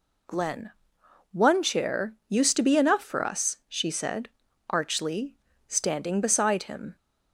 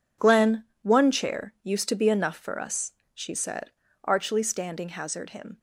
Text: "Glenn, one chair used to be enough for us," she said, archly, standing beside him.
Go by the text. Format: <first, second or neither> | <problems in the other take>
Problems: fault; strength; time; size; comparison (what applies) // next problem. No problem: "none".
first | says "hazard" for "beside"; at 4.8 s